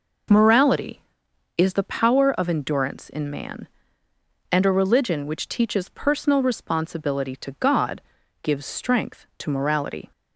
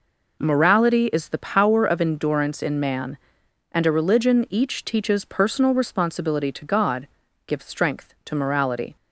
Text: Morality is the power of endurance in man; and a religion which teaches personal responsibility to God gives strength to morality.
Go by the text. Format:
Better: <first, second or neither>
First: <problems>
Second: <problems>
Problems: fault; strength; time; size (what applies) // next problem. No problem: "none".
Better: first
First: pauses between "God" and "gives"; at 7.9 s; 0.44 s long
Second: says "each" for "which"; at 4.4 s // pauses between "God" and "gives"; at 7.0 s; 0.40 s long